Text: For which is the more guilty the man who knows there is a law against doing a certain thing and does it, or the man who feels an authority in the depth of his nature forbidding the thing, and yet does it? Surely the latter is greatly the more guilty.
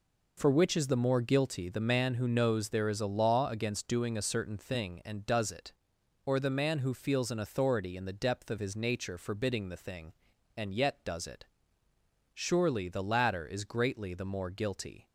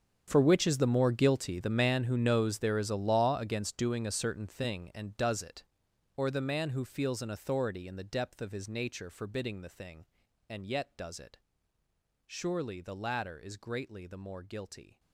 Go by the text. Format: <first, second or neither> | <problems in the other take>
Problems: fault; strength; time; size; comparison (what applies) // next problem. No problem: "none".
first | gets quieter; strong; throughout; 17.5 dB